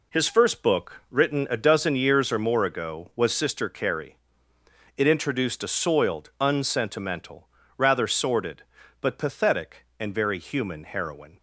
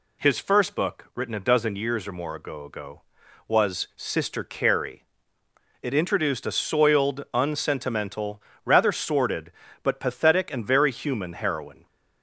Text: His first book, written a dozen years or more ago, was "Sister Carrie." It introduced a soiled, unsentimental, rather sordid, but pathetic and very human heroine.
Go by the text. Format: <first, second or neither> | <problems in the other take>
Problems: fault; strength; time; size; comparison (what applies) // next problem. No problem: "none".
first | says "ago" twice; at 2.6 s